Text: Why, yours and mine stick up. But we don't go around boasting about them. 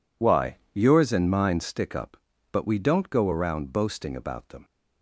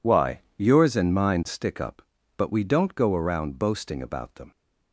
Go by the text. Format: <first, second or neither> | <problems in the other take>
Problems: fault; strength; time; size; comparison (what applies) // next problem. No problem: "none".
neither | none